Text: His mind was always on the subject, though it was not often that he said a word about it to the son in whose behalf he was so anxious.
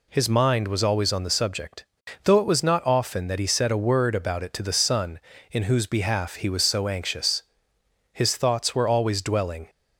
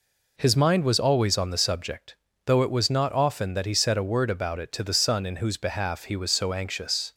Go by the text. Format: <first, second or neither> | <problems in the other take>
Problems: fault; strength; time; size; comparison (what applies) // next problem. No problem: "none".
second | goes on to say "His thoughts were always dwelling"; from 8.1 s on; 1.5 s long